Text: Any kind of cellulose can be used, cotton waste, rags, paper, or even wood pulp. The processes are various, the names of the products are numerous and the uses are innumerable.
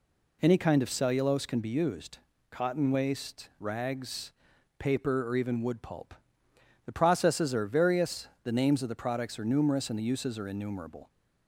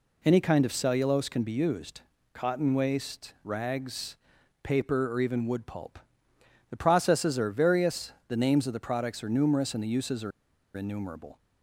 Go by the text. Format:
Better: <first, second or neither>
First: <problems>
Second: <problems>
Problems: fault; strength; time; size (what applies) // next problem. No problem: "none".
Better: first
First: none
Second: pauses between "are" and "innumerable"; at 10.3 s; 0.44 s long